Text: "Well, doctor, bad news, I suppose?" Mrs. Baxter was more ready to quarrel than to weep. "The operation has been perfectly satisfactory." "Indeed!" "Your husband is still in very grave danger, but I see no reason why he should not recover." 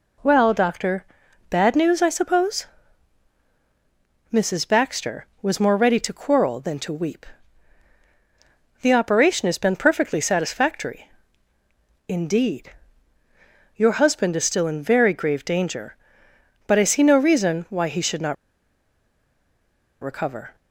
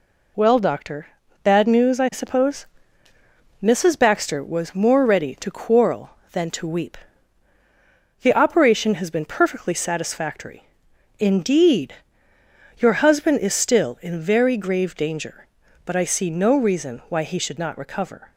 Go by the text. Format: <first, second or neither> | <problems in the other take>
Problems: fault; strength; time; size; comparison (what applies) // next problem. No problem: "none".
second | pauses between "not" and "recover"; strong; at 18.3 s; 1.6 s long